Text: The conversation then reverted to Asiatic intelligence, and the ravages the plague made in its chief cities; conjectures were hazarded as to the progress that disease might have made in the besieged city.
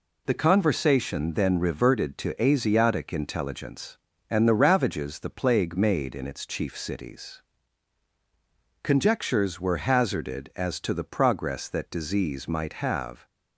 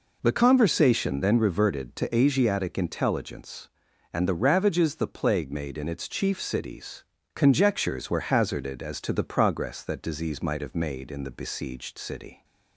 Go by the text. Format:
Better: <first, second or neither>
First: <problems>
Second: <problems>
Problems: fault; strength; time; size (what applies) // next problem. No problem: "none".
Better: second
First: stops before "made in the besieged city"; at 13.2 s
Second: none